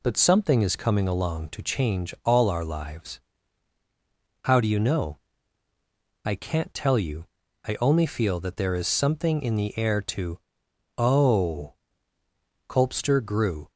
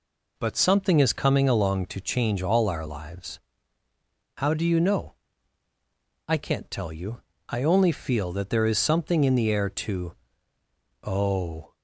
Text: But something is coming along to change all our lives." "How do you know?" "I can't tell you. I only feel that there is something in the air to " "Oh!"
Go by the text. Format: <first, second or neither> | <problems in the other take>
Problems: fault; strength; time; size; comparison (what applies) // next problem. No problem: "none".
second | goes on to say "Colpster grew"; noticeable; from 12.6 s on; 1.0 s long